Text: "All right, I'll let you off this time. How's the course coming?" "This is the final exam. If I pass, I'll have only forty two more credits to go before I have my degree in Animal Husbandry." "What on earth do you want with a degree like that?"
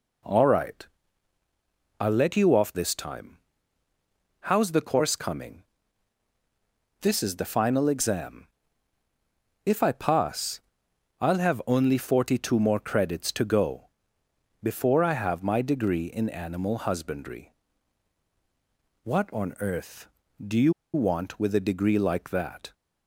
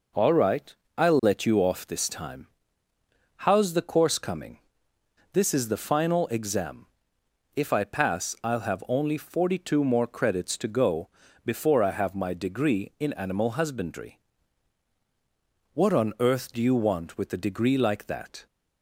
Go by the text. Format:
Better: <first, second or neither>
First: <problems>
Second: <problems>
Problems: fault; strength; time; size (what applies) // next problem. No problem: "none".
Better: second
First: pauses between "go" and "before"; noticeable; at 13.8 s; 0.72 s long // pauses between "you" and "want"; slight; at 20.7 s; 0.21 s long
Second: pauses between "go" and "before"; slight; at 11.1 s; 0.34 s long